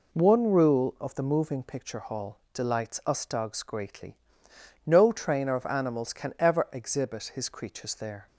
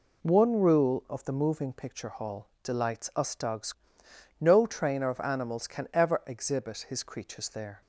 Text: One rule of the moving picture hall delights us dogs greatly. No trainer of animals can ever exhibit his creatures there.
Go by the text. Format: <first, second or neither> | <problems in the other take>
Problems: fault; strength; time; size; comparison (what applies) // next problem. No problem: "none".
first | pauses between "hall" and "delights"; slight; at 2.4 s; 0.16 s long; slight in the first // skips "greatly"; at 4.0 s